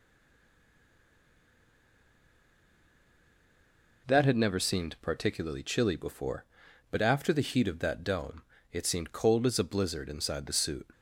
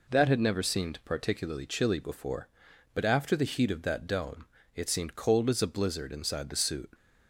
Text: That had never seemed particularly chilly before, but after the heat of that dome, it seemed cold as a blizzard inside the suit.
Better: second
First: stays silent before the first word; strong; until 4.0 s; 4.0 s long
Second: none

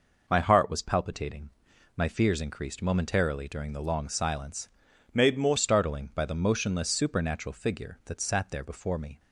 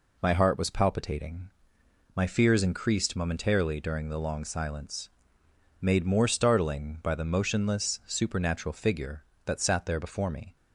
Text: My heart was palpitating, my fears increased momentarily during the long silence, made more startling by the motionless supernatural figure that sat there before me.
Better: second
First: changes voice from "made" to "more"; from 5.1 to 5.5 s; 0.4 s long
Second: none

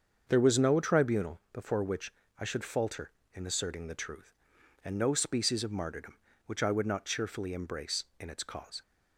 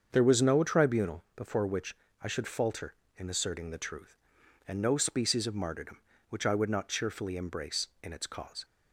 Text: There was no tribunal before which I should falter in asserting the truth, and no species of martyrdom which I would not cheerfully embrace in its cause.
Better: neither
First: starts louder than the rest; until 1.2 s; 7 dB // pauses between "which" and "I"; slight; at 2.1 s; 0.28 s long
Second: starts louder than the rest; until 1.1 s; 7 dB // pauses between "which" and "I"; slight; at 1.9 s; 0.28 s long

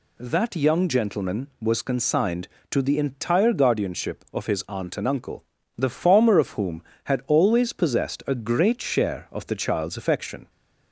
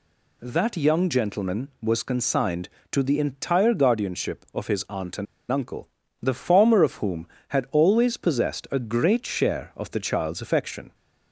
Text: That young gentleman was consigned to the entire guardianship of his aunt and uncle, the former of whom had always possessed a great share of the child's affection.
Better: first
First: none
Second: pauses between "and" and "uncle"; slight; at 5.2 s; 0.26 s long

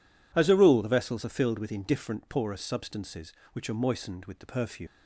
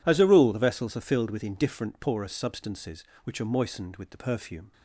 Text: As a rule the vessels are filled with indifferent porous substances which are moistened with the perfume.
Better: second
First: leaves "perfume" unfinished; at 4.8 s; 140 ms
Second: none

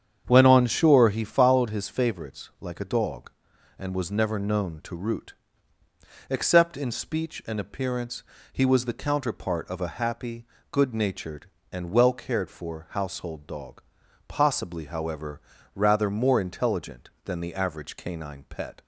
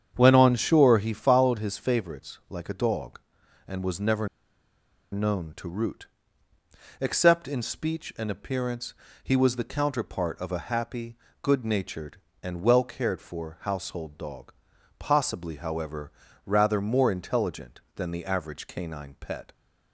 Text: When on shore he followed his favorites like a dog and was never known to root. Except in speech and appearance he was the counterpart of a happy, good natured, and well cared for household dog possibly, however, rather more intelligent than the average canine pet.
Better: first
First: starts louder than the rest; strong; until 1.2 s; 8 dB // pauses between "appearance" and "he"; slight; at 8.2 s; 0.28 s long // pauses between "dog" and "possibly"; noticeable; at 13.8 s; 0.46 s long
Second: starts louder than the rest; strong; until 1.1 s; 8 dB // pauses between "never" and "known"; noticeable; at 4.2 s; 0.84 s long // pauses between "appearance" and "he"; slight; at 8.9 s; 0.28 s long // pauses between "dog" and "possibly"; noticeable; at 14.5 s; 0.46 s long

